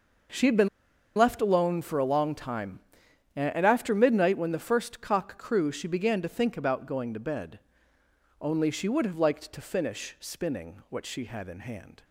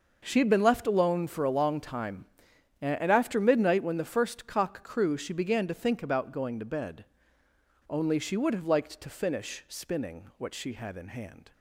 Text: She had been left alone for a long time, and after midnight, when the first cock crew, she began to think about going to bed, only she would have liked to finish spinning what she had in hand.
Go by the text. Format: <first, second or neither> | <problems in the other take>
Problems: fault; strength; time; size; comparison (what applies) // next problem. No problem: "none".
second | pauses between "been" and "left"; noticeable; at 0.6 s; 0.49 s long